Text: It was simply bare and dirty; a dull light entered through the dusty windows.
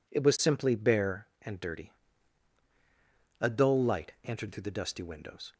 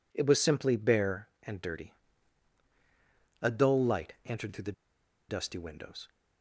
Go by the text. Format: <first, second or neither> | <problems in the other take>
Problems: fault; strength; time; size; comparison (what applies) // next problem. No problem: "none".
first | pauses between "the" and "dusty"; noticeable; at 4.7 s; 0.56 s long